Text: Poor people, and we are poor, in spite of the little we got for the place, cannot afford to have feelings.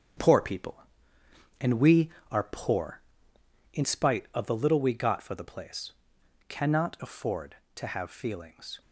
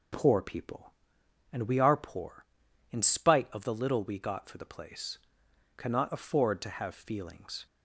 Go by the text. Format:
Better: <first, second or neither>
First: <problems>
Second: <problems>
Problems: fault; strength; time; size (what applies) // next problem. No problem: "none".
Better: second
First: gets quieter; throughout; 6.5 dB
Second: none